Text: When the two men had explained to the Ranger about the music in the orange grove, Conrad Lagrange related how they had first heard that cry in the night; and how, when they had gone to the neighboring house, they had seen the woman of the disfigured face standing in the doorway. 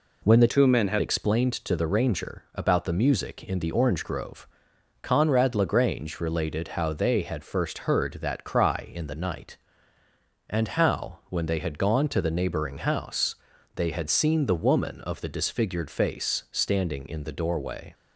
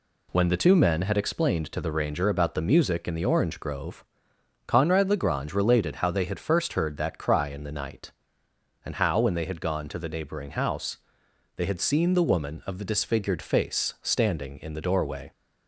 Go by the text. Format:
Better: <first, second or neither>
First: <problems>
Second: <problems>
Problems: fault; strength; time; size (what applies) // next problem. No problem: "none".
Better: second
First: changes voice from "two" to "had"; from 0.4 to 1.0 s; 0.6 s long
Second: none